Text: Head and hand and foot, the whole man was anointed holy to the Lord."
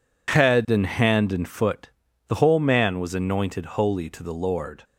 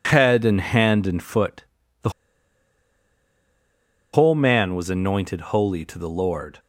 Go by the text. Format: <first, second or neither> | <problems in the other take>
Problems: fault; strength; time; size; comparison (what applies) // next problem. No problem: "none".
first | pauses between "the" and "whole"; strong; at 2.0 s; 2.0 s long